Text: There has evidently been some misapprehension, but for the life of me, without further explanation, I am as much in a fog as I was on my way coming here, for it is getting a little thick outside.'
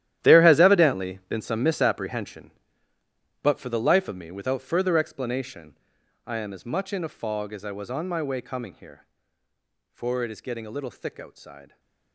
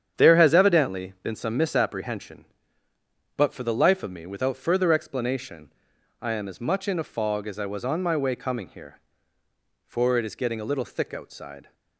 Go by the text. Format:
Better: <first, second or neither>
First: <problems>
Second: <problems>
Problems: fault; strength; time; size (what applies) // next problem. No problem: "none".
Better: second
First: gets quieter; strong; throughout; 16.5 dB // starts louder than the rest; strong; until 1.3 s; 12 dB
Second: starts louder than the rest; strong; until 1.2 s; 8.5 dB